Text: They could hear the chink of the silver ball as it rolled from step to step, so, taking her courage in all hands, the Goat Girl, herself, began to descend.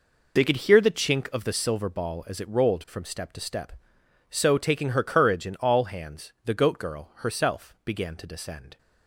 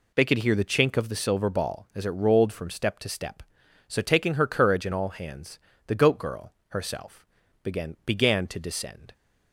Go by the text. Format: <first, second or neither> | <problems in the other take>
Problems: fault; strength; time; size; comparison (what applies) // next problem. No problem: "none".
first | says "began" twice; at 8.0 s